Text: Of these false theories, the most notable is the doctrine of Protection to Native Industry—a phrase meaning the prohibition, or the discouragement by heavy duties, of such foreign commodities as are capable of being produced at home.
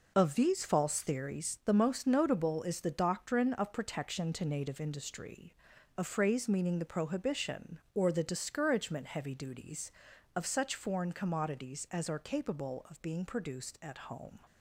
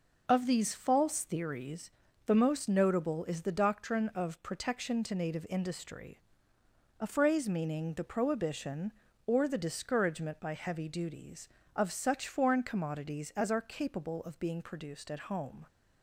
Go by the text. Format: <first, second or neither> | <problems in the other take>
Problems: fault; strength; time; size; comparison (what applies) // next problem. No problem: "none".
second | skips "by"; at 9.0 s